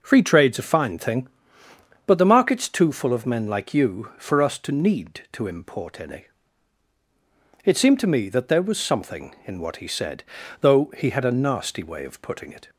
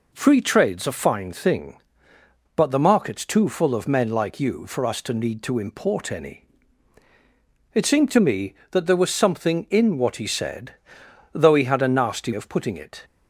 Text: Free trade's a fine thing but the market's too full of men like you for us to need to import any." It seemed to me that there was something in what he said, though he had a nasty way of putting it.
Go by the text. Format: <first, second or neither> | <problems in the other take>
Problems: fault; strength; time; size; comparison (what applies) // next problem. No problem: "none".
first | skips "way"; at 12.3 s